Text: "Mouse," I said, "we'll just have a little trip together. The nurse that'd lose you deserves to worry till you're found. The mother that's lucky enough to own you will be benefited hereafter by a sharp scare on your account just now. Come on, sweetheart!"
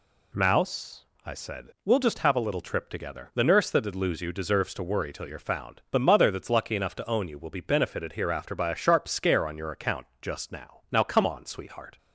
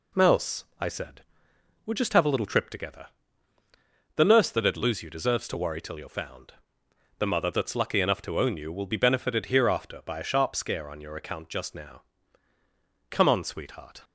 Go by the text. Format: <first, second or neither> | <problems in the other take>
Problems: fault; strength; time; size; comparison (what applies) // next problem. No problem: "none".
second | says "now" twice; at 10.9 s